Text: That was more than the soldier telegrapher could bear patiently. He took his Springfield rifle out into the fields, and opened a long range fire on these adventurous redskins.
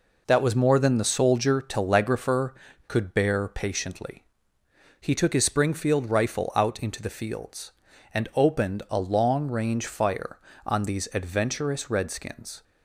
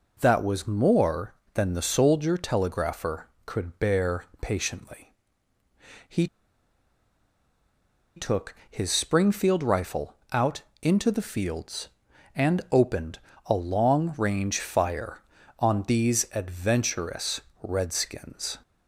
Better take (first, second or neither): first